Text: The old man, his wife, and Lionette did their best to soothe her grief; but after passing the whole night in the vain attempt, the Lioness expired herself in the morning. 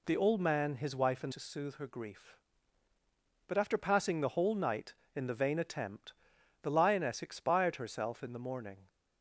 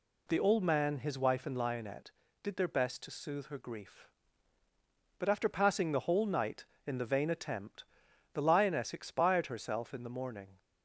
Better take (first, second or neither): second